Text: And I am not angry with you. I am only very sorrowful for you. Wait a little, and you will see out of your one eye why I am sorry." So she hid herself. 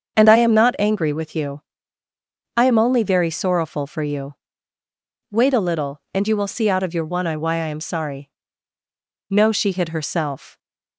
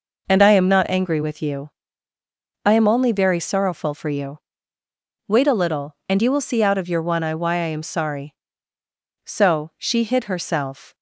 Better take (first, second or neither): second